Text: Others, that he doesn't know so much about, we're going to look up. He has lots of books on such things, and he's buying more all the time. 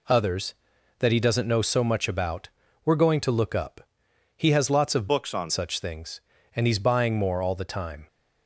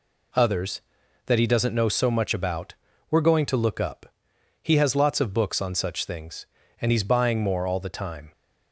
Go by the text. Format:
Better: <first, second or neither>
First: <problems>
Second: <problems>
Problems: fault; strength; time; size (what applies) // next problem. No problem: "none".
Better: second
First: changes voice from "books" to "on"; from 5.0 to 5.5 s; 0.5 s long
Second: none